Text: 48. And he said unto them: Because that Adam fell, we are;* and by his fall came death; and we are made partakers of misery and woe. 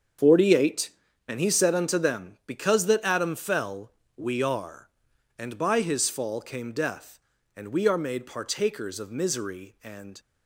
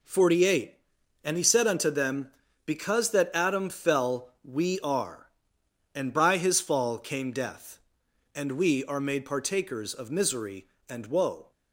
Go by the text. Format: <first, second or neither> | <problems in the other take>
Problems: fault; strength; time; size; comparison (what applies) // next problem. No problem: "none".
second | starts louder than the rest; strong; until 1.6 s; 7.5 dB // stops before "woe"; at 10.1 s